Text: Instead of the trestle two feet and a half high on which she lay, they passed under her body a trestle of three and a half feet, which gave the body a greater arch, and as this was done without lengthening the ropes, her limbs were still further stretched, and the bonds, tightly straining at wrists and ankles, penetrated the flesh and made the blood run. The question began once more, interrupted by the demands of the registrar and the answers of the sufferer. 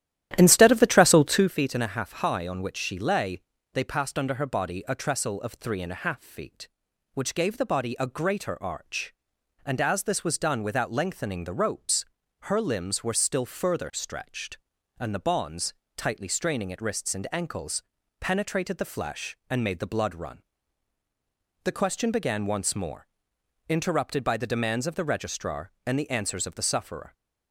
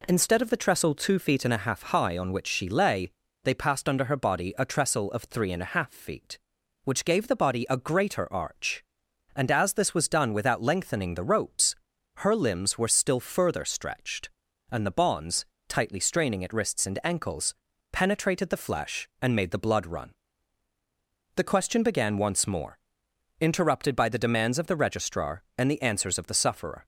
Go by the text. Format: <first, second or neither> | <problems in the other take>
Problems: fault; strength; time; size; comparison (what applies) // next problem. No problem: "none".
second | starts louder than the rest; strong; until 1.6 s; 12.5 dB